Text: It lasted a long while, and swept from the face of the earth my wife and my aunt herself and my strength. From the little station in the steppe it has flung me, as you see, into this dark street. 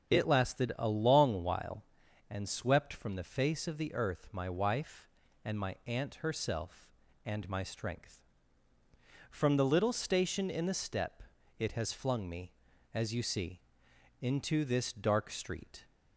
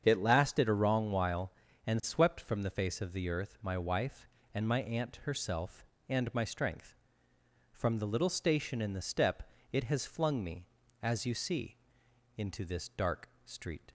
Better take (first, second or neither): first